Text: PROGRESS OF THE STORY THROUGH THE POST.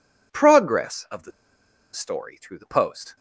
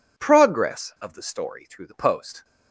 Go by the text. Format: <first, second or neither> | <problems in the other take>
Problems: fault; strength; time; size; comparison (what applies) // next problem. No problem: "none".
second | pauses between "THE" and "STORY"; noticeable; at 1.3 s; 0.62 s long